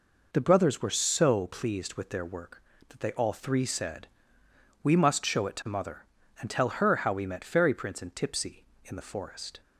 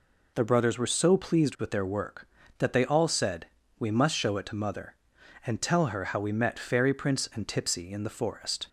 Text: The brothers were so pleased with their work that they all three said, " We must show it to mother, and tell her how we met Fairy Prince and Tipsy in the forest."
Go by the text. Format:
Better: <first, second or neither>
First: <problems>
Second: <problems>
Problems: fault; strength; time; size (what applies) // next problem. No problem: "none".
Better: first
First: none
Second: skips "three"; at 3.0 s